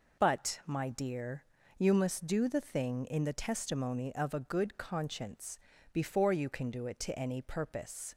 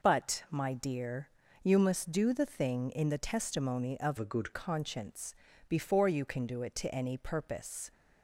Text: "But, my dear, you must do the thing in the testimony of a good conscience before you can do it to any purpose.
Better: first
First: pauses between "conscience" and "before"; slight; at 5.5 s; 0.34 s long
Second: changes voice from "a" to "good"; from 4.1 to 4.5 s; 0.4 s long // pauses between "conscience" and "before"; slight; at 5.3 s; 0.34 s long

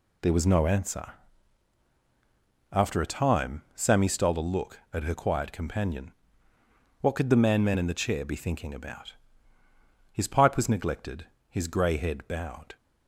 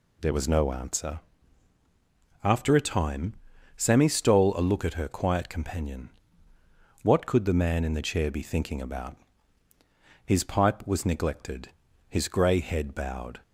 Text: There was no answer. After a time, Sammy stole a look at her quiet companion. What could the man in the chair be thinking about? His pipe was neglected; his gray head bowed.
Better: second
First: says "man" twice; at 7.6 s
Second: none

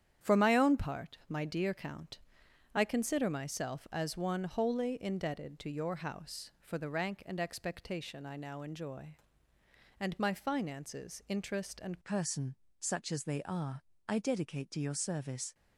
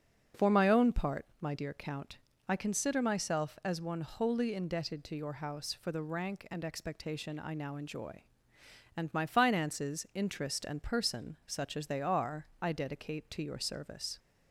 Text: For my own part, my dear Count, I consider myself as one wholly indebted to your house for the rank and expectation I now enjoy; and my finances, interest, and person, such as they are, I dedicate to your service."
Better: second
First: starts louder than the rest; strong; until 1.3 s; 9 dB // changes voice at "person"; from 12.0 s on; 3.5 s long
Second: starts louder than the rest; until 1.5 s; 6.5 dB

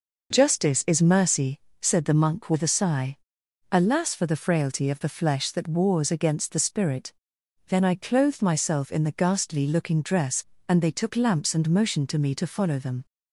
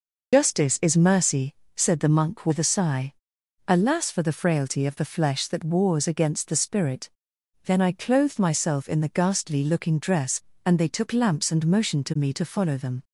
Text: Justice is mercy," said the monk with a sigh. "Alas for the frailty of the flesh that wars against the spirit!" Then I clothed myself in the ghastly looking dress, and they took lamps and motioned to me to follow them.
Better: first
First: none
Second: loses the start of "Justice"; at 0.3 s; 75 ms

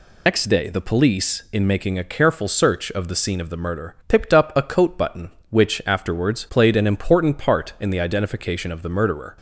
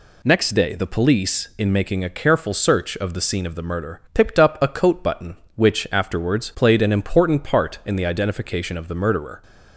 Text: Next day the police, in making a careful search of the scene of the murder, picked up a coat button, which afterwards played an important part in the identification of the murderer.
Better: second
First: loses the start of "Next"; at 0.2 s; 75 ms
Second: none

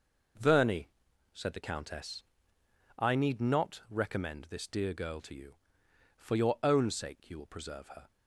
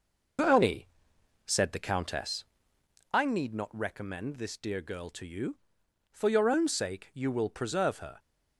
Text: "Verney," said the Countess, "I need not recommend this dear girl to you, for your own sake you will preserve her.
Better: first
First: none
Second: loses the start of "Verney"; at 0.3 s; 105 ms

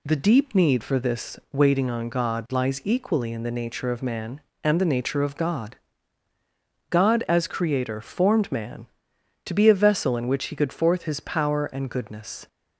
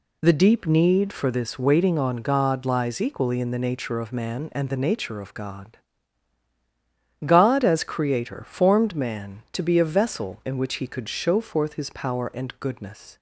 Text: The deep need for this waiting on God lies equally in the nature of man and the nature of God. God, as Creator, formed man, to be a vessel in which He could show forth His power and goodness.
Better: second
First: skips "show"; at 10.7 s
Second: none

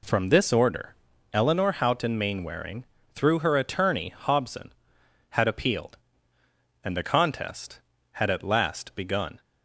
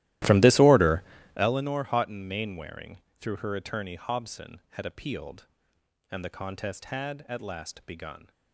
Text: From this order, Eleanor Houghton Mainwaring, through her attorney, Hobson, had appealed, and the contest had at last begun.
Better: first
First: none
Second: starts louder than the rest; strong; until 1.5 s; 15.5 dB

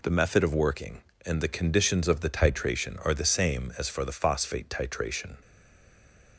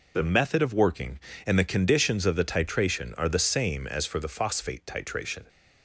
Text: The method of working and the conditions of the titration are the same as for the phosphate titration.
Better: second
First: stays silent after the last word; from 5.4 s on; 0.9 s long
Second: none

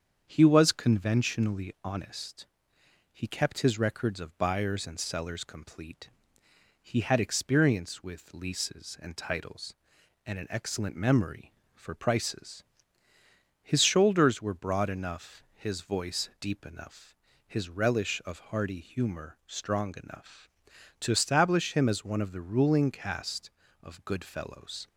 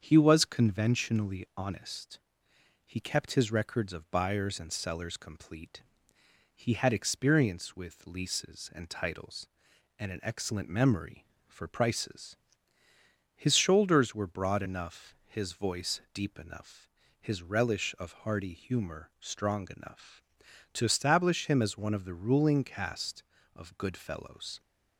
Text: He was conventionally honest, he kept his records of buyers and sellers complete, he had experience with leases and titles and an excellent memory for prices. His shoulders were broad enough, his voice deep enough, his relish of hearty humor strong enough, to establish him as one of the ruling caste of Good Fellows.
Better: neither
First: starts louder than the rest; strong; until 1.2 s; 7.5 dB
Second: starts louder than the rest; strong; until 1.0 s; 7.5 dB

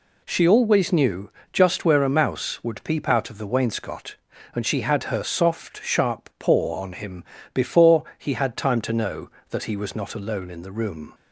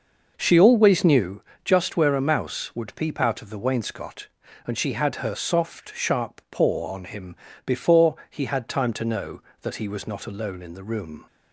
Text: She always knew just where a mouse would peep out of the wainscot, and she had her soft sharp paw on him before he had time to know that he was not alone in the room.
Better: first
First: pauses between "knew" and "just"; slight; at 1.3 s; 0.22 s long // pauses between "him" and "before"; slight; at 7.2 s; 0.28 s long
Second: starts louder than the rest; noticeable; until 1.3 s; 6 dB // pauses between "knew" and "just"; slight; at 1.4 s; 0.22 s long // pauses between "him" and "before"; slight; at 7.3 s; 0.28 s long

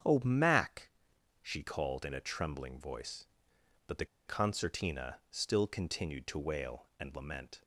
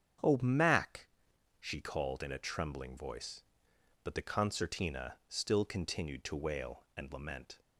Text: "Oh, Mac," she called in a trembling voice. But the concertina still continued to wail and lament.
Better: second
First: starts louder than the rest; strong; until 1.6 s; 8 dB // pauses between "the" and "concertina"; slight; at 4.0 s; 0.21 s long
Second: starts louder than the rest; strong; until 1.8 s; 7.5 dB

